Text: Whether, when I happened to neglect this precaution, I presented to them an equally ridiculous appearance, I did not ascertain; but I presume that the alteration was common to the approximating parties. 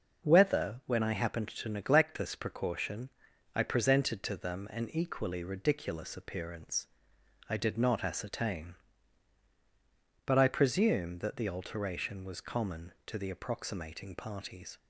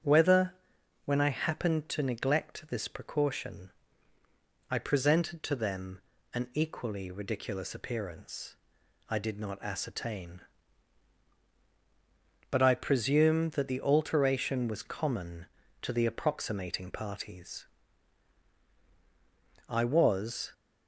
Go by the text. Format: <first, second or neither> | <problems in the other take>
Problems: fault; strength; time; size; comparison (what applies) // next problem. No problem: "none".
first | starts louder than the rest; strong; until 1.5 s; 8 dB // pauses between "them" and "an"; slight; at 6.0 s; 0.34 s long // goes on to say "I was"; noticeable; from 19.6 s on; 0.82 s long